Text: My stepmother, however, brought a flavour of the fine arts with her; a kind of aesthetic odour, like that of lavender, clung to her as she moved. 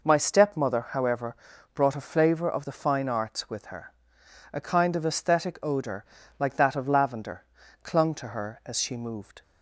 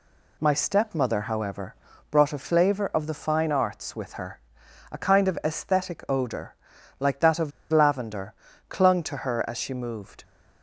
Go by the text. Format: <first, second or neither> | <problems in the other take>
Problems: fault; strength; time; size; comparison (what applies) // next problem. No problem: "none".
first | pauses between "of" and "lavender"; slight; at 7.5 s; 0.21 s long